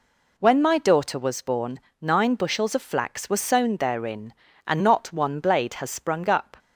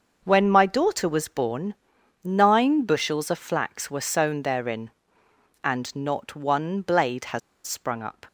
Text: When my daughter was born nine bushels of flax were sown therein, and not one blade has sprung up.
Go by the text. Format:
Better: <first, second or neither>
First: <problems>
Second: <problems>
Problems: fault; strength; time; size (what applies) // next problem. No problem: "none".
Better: first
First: pauses between "born" and "nine"; slight; at 1.7 s; 0.22 s long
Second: starts louder than the rest; until 1.2 s; 6 dB // pauses between "born" and "nine"; noticeable; at 1.7 s; 0.48 s long // pauses between "has" and "sprung"; slight; at 7.4 s; 0.26 s long